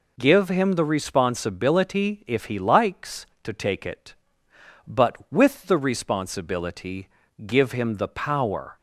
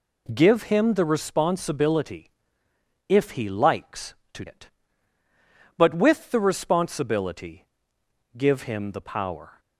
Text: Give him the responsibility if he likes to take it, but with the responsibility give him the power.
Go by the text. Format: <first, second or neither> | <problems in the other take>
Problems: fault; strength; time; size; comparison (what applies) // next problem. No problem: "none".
first | pauses between "responsibility" and "if"; noticeable; at 2.3 s; 0.76 s long // skips "take"; at 4.4 s // pauses between "responsibility" and "give"; noticeable; at 7.6 s; 0.68 s long; also in the first